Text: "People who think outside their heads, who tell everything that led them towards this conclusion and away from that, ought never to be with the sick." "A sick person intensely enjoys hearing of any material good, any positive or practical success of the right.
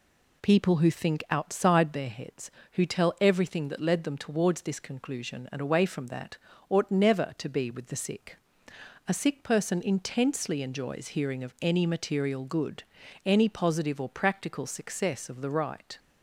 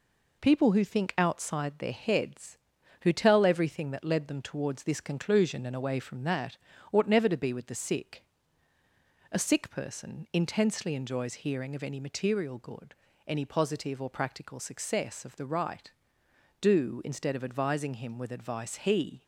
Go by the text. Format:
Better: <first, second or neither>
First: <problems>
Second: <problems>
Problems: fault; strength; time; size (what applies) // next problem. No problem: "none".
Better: first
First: none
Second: goes on to say "Do instead of advising him with advice he"; strong; from 16.5 s on; 2.6 s long